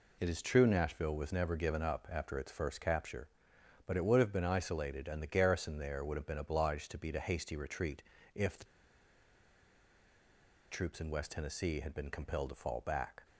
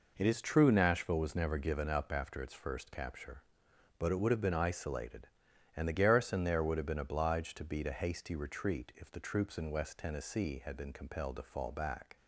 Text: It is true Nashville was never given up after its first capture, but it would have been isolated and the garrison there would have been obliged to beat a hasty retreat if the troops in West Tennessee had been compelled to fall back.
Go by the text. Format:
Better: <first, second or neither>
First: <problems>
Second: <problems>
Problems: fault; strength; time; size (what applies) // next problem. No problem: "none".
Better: second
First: pauses between "retreat" and "if"; slight; at 8.0 s; 0.32 s long // pauses between "the" and "troops"; strong; at 8.6 s; 2.0 s long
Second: none